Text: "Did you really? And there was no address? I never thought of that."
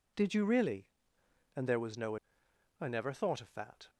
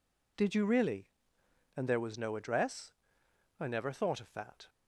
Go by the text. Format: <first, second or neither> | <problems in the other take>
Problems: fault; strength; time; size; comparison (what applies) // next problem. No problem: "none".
second | skips "address"; at 2.4 s